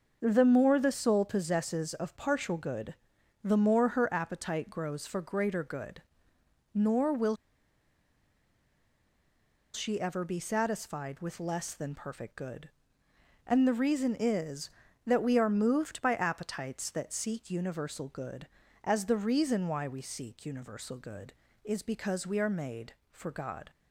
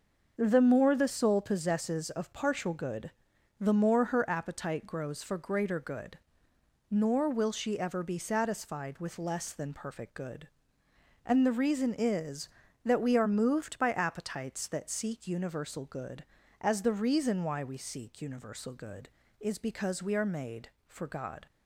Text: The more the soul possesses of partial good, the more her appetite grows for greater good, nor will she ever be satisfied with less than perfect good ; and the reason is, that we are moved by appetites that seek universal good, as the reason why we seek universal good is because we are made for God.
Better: second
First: starts louder than the rest; until 1.2 s; 6 dB // pauses between "will" and "she"; strong; at 7.3 s; 2.3 s long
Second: starts louder than the rest; until 1.3 s; 6 dB

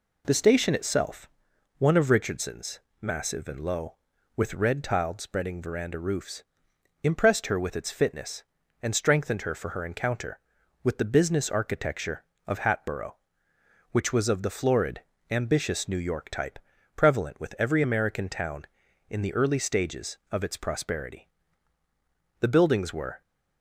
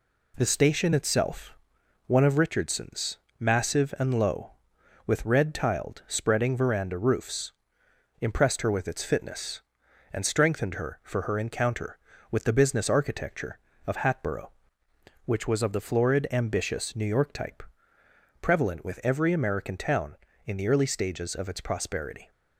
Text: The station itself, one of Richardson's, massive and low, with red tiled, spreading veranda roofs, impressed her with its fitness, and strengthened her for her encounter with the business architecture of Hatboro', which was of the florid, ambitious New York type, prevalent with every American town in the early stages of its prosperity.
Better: second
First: goes on to say "The buildings were"; noticeable; from 22.3 s on; 0.82 s long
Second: none

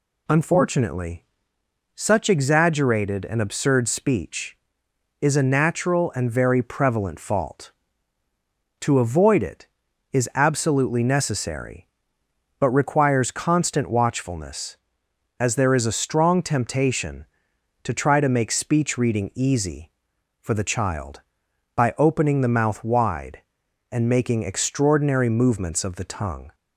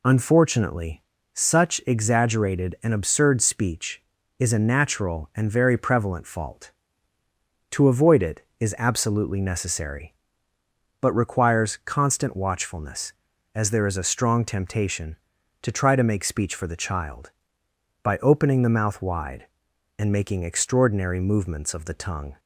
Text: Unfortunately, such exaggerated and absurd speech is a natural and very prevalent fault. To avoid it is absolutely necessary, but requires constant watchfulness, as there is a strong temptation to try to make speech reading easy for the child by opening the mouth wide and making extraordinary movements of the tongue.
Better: first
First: none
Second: skips "reading easy"; at 16.5 s

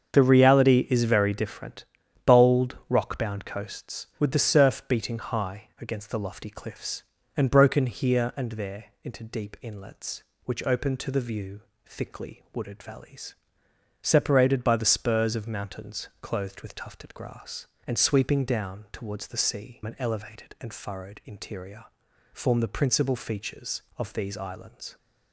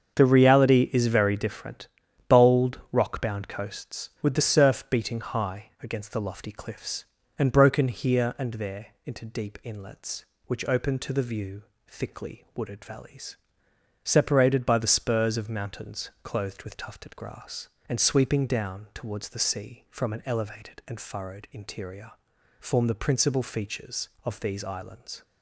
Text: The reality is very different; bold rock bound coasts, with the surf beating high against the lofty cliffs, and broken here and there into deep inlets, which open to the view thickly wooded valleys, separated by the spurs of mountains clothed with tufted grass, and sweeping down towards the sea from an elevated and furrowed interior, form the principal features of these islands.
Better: second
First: starts louder than the rest; until 1.1 s; 7 dB // pauses between "there" and "into"; slight; at 8.8 s; 0.18 s long // pauses between "view" and "thickly"; slight; at 11.6 s; 0.24 s long // skips "from"; at 19.8 s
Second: starts louder than the rest; until 1.1 s; 7 dB // pauses between "there" and "into"; slight; at 8.8 s; 0.18 s long // pauses between "view" and "thickly"; slight; at 11.6 s; 0.24 s long

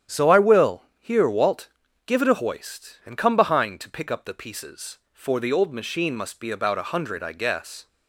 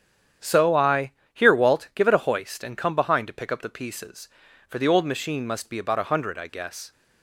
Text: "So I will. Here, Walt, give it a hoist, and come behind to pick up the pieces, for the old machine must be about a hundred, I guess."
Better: first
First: starts louder than the rest; strong; until 1.2 s; 9.5 dB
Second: starts louder than the rest; strong; until 1.6 s; 9 dB // skips "will"; at 1.2 s

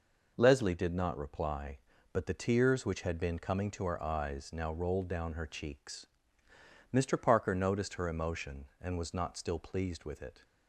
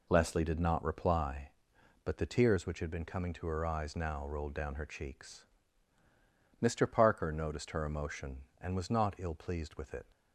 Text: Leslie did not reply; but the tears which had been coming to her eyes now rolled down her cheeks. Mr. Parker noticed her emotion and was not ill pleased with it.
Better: second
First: says "still" for "ill"; at 9.3 s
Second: none

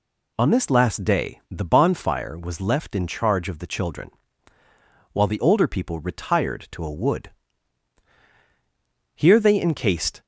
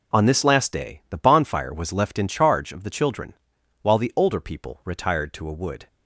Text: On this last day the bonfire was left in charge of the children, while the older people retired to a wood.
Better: second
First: goes on to say "Here they encased"; noticeable; from 9.1 s on; 1.1 s long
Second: none

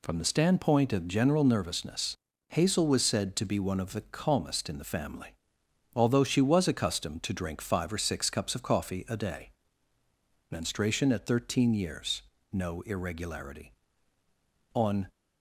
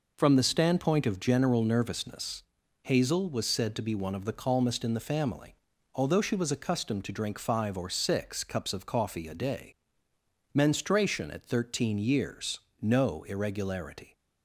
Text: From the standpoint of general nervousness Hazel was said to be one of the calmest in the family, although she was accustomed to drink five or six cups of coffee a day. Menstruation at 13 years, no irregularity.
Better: second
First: pauses between "nervousness" and "Hazel"; slight; at 2.1 s; 0.34 s long // goes on to say "On"; slight; from 14.7 s on; 0.36 s long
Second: pauses between "nervousness" and "Hazel"; at 2.4 s; 0.38 s long

